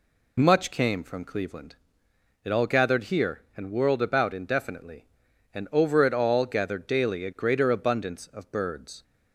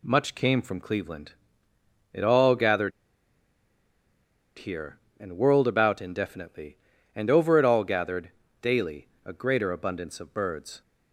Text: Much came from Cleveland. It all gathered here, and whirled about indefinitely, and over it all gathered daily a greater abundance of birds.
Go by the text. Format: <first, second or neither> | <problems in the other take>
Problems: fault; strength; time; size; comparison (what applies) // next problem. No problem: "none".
first | pauses between "gathered" and "here"; strong; at 2.9 s; 1.6 s long // pauses between "gathered" and "daily"; slight; at 8.3 s; 0.32 s long // pauses between "daily" and "a"; slight; at 9.0 s; 0.16 s long